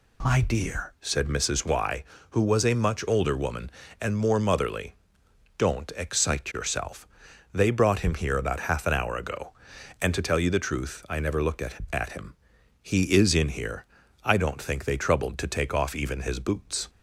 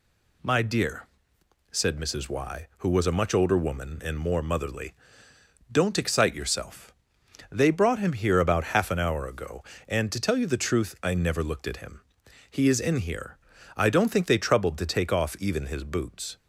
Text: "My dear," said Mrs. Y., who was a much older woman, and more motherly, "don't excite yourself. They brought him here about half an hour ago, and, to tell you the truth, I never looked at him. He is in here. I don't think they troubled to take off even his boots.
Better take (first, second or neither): second